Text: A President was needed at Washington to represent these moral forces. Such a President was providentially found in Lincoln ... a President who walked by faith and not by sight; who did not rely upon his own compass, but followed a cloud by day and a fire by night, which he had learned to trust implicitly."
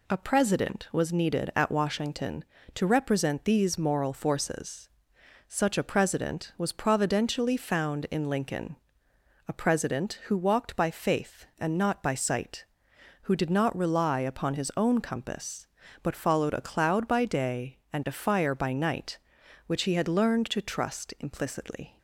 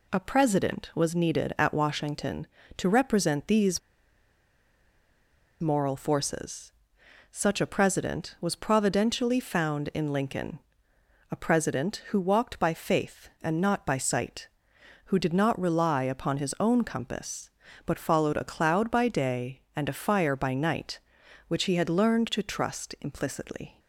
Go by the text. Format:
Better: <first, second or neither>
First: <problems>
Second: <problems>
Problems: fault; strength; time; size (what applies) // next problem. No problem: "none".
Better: first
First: none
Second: pauses between "these" and "moral"; strong; at 3.7 s; 1.8 s long